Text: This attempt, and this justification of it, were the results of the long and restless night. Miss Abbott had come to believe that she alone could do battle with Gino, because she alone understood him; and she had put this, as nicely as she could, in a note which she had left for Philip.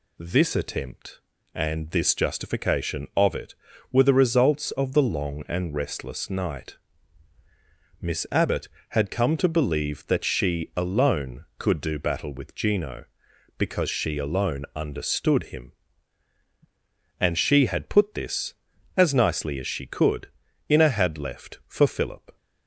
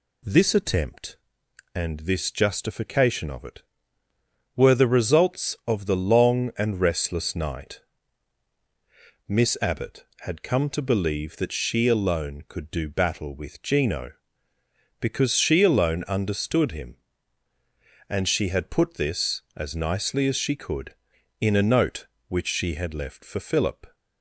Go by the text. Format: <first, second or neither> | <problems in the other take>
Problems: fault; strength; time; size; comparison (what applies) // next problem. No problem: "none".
second | skips "note which she"; at 20.9 s